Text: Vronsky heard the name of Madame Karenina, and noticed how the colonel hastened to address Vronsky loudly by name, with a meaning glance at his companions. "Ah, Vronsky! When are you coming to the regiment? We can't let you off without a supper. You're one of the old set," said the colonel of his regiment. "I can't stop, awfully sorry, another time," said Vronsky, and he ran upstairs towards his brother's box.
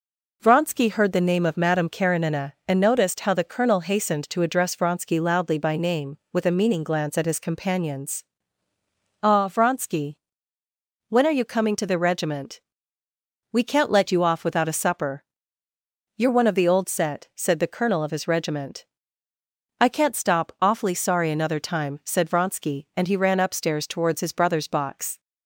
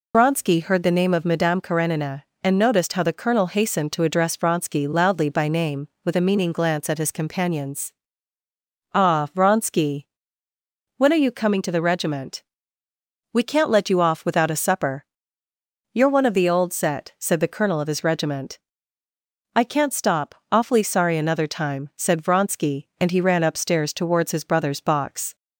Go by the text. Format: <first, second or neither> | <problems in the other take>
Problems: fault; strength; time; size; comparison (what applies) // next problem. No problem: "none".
first | loses the start of "Vronsky"; at 0.1 s; 55 ms